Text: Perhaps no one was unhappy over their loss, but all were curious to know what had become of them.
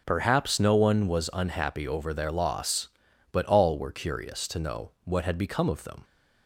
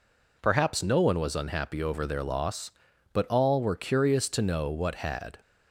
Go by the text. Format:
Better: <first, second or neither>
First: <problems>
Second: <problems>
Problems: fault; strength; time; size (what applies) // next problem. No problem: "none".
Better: first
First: none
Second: stops before "become of them"; at 5.4 s